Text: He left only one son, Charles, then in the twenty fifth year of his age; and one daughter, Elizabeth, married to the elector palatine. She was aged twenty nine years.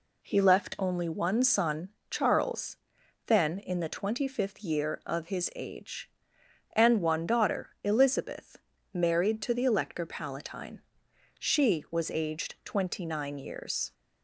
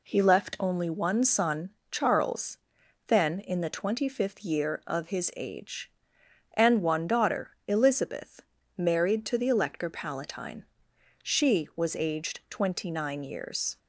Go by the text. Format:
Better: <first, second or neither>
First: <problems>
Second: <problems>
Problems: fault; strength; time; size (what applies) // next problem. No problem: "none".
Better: neither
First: none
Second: none